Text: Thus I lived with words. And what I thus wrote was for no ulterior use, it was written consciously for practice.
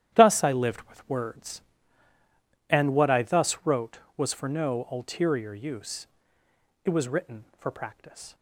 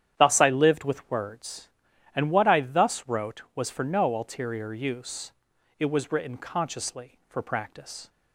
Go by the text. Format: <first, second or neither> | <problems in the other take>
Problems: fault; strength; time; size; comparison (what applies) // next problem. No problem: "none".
second | starts louder than the rest; strong; until 1.1 s; 11.5 dB; strong in the second // skips "consciously"; at 7.5 s